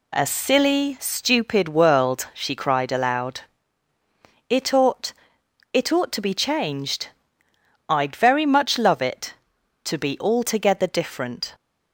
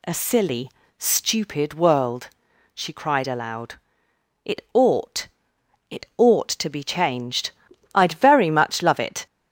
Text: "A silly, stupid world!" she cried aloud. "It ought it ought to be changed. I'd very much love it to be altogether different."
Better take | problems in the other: first | pauses between "ought" and "it"; noticeable; at 5.2 s; 0.64 s long; noticeable in the first // stops before "to be altogether different"; at 9.2 s

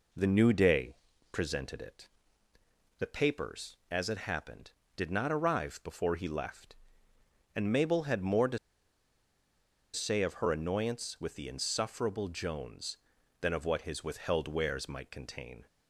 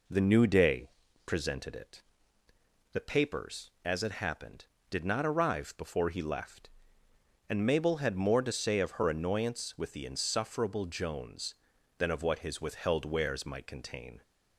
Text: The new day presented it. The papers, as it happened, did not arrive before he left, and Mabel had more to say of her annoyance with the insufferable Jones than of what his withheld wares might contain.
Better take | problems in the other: second | pauses between "day" and "presented"; slight; at 0.9 s; 0.36 s long; slight in the second // pauses between "to" and "say"; strong; at 8.5 s; 1.3 s long

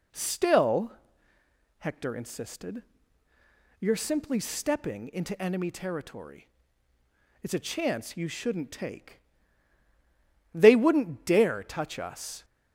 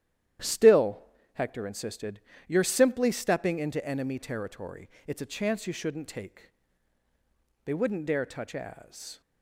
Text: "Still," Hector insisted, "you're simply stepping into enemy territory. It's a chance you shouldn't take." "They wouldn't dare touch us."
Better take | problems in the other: first | starts louder than the rest; strong; until 1.7 s; 11.5 dB // says "as" for "us"; at 8.5 s

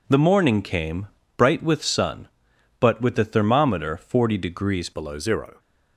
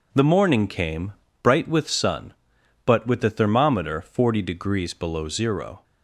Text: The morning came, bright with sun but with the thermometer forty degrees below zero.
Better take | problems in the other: second | changes voice at "below"; from 4.9 s on; 0.6 s long

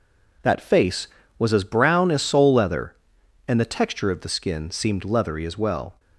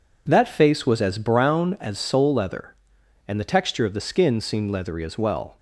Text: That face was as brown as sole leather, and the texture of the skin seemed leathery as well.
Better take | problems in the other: neither | none

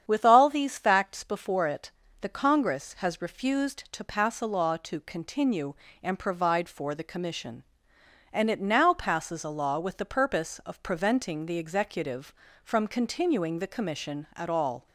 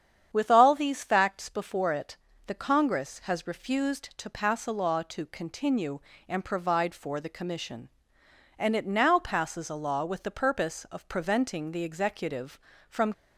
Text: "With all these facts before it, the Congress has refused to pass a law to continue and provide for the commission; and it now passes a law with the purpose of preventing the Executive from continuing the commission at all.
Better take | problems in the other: first | starts louder than the rest; strong; until 1.3 s; 8.5 dB; strong in the first // stops before "continuing the commission at all"; at 13.1 s

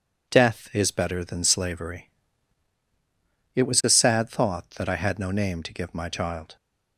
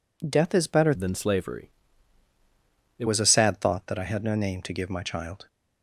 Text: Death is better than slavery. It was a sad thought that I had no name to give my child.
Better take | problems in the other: first | changes voice from "than" to "It"; from 0.9 to 3.0 s; 2.1 s long

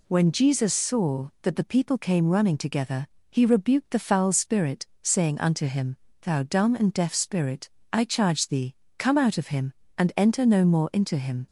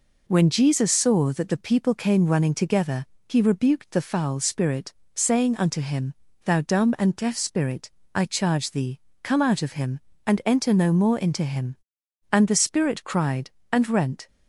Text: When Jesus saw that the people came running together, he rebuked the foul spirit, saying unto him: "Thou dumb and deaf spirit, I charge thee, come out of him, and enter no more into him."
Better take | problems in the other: first | goes on to say "And the spirit cried and rent"; strong; from 12.3 s on; 1.9 s long

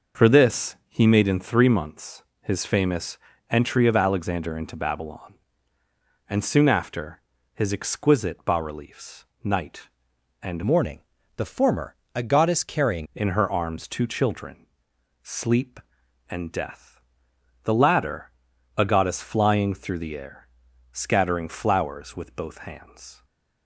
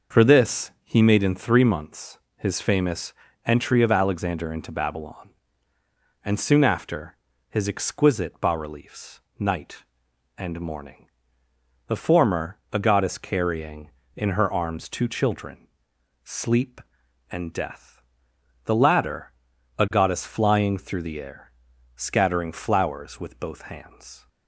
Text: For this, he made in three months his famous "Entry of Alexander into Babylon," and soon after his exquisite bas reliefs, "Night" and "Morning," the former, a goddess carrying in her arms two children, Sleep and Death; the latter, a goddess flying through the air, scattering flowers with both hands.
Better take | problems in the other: second | pauses between "months" and "his"; slight; at 2.2 s; 0.18 s long; slight in the second // pauses between "famous" and "Entry"; slight; at 3.1 s; 0.32 s long; slight in the second // pauses between "after" and "his"; slight; at 7.1 s; 0.32 s long; slight in the second // changes voice from "Morning" to "carrying"; from 10.6 to 13.0 s; 2.4 s long // stays silent after the last word; slight; from 23.1 s on; 0.5 s long

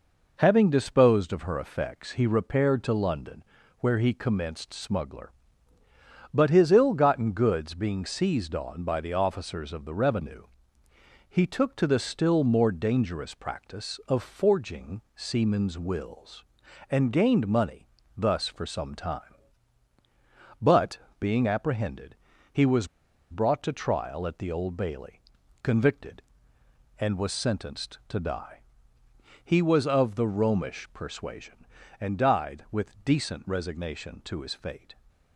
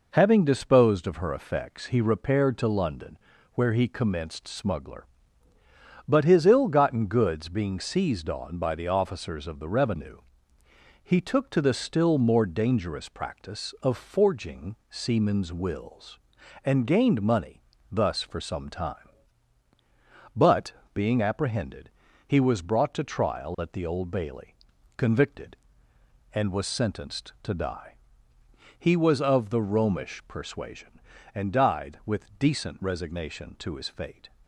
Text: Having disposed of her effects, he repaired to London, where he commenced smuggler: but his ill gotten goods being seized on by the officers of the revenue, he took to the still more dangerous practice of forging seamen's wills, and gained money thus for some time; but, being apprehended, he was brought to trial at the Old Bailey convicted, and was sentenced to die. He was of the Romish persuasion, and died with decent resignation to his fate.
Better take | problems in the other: second | pauses between "money" and "thus"; slight; at 17.8 s; 0.28 s long; slight in the second // pauses between "was" and "brought"; at 22.8 s; 0.43 s long // pauses between "Bailey" and "convicted"; at 25.2 s; 0.42 s long; also in the second

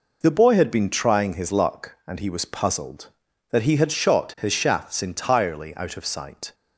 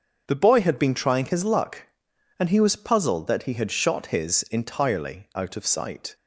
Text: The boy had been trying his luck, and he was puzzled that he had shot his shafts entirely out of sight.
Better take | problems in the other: first | starts louder than the rest; until 1.2 s; 6.5 dB // skips "shafts"; at 4.4 s

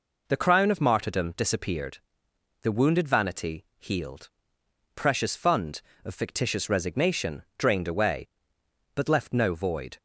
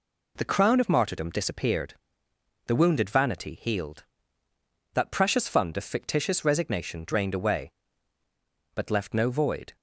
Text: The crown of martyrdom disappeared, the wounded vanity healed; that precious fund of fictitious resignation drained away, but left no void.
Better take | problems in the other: second | skips "that"; at 4.6 s // pauses between "resignation" and "drained"; slight; at 7.4 s; 0.16 s long

